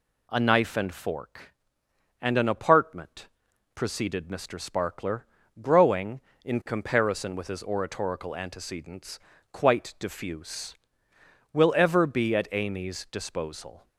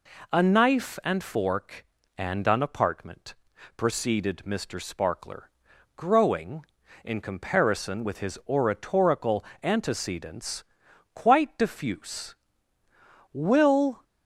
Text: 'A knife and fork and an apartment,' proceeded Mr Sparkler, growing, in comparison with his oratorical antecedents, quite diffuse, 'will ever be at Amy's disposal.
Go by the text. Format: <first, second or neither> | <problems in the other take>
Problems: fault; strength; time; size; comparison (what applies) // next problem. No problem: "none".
first | pauses between "oratorical" and "antecedents"; slight; at 9.4 s; 0.20 s long // stops before "ever be at Amy's disposal"; at 14.0 s